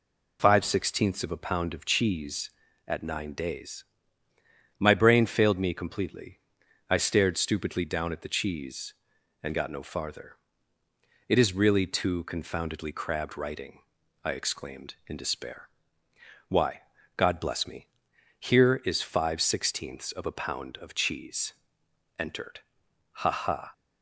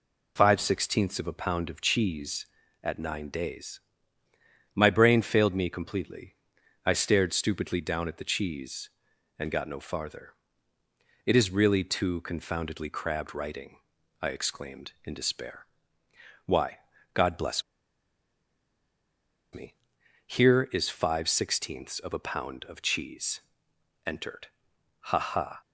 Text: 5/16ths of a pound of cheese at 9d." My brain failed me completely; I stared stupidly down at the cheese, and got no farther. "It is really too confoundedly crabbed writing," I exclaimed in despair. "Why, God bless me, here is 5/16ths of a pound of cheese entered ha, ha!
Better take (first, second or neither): first